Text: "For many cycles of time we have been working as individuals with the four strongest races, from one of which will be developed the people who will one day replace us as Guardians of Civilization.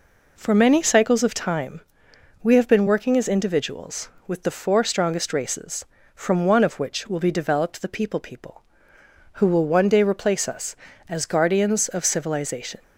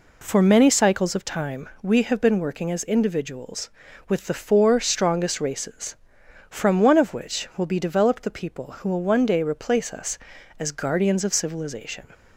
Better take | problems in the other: second | pauses between "time" and "we"; noticeable; at 1.8 s; 0.62 s long // says "people" twice; at 8.1 s

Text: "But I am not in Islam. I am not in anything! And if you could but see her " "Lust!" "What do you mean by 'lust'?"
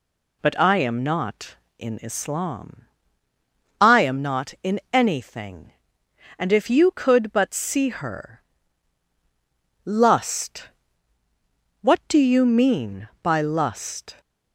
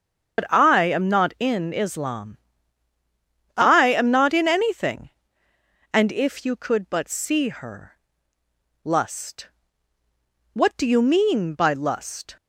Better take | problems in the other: first | loses the start of "But"; at 0.3 s; 90 ms // starts louder than the rest; strong; until 1.4 s; 7 dB

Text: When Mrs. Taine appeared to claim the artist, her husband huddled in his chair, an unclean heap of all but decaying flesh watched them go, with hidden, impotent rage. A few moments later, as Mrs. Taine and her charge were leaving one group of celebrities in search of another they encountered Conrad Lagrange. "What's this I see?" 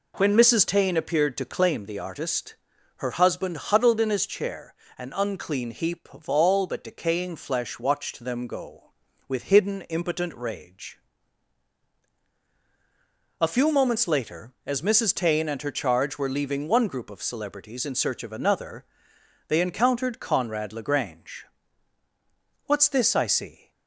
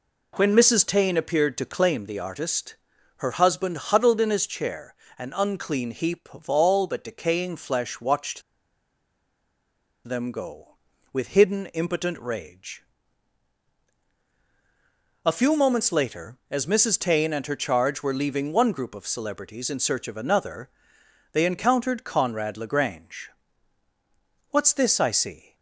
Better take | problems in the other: first | pauses between "watched" and "them"; strong; at 8.4 s; 1.6 s long // pauses between "another" and "they"; noticeable; at 20.6 s; 0.64 s long; noticeable in the first

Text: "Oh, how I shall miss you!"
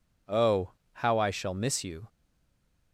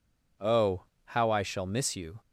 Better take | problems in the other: second | stays silent after the last word; slight; from 2.0 s on; 0.9 s long

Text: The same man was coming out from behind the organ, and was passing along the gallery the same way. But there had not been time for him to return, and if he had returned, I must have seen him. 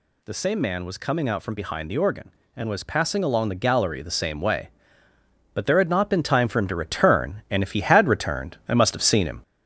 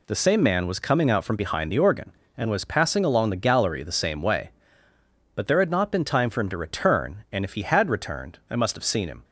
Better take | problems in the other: second | gets louder; throughout; 3.5 dB

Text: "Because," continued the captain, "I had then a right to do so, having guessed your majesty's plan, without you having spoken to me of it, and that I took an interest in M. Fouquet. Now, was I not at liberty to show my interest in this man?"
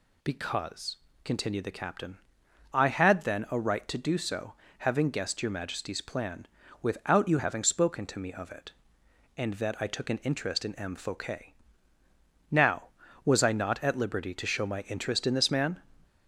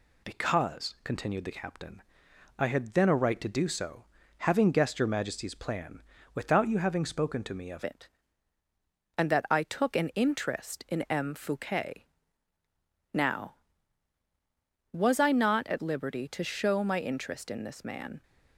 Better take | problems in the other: first | changes voice at "it"; from 7.8 s on; 10.4 s long

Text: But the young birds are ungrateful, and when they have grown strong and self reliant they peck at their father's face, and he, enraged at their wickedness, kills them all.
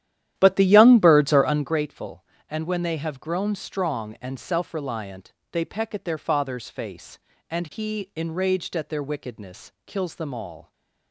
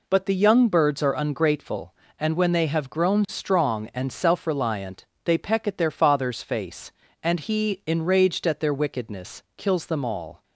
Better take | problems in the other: second | starts louder than the rest; strong; until 1.8 s; 11.5 dB // pauses between "reliant" and "they"; slight; at 5.3 s; 0.20 s long; slight in the second

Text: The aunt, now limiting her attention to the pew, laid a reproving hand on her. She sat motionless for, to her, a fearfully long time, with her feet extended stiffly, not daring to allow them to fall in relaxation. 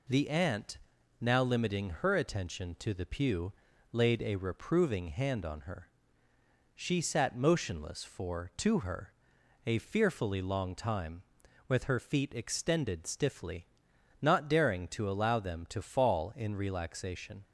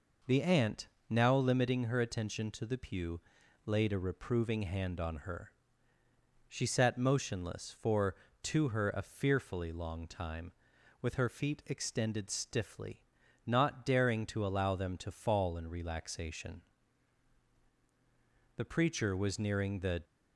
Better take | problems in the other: first | goes on to say "The preacher was nearing the"; from 18.5 s on; 1.4 s long

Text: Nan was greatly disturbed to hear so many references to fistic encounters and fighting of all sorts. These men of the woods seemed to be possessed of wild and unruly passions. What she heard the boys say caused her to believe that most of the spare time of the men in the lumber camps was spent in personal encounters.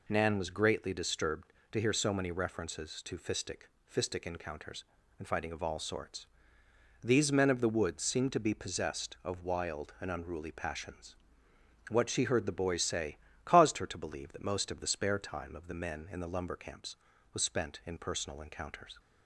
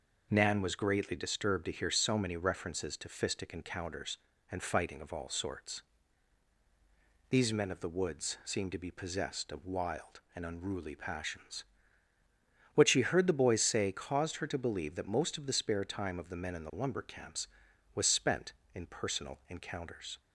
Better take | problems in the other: second | says "fistic" twice; at 3.9 s // pauses between "say" and "caused"; slight; at 13.1 s; 0.28 s long

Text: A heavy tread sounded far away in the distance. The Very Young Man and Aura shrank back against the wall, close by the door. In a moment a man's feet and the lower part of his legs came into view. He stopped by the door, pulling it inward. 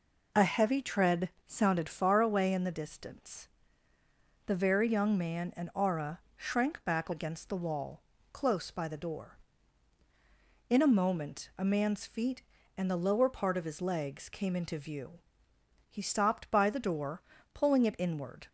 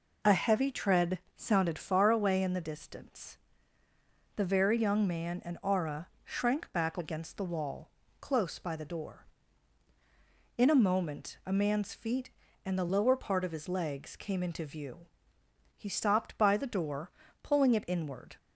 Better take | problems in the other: neither | pauses between "tread" and "sounded"; slight; the same in both // pauses between "Aura" and "shrank"; slight; the same in both

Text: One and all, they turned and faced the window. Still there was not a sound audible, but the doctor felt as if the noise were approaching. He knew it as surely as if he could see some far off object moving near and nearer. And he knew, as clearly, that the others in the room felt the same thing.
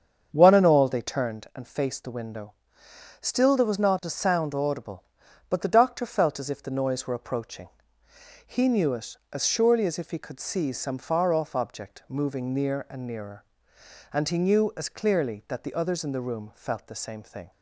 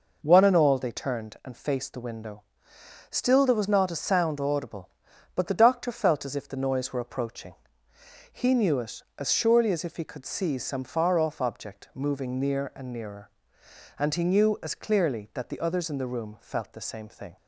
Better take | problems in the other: second | starts louder than the rest; strong; until 1.4 s; 7.5 dB

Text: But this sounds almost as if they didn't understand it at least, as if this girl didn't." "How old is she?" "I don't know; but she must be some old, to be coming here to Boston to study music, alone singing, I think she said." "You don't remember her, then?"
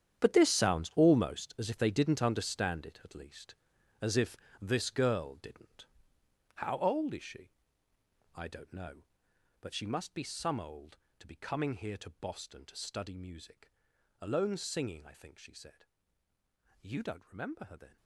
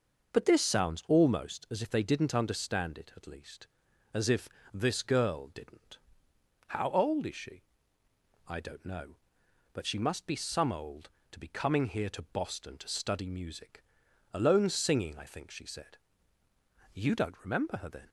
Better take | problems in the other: second | gets quieter; strong; throughout; 14 dB // starts louder than the rest; strong; until 1.2 s; 9.5 dB; noticeable in the second // pauses between "if" and "this"; slight; at 4.3 s; 0.24 s long; slight in the second

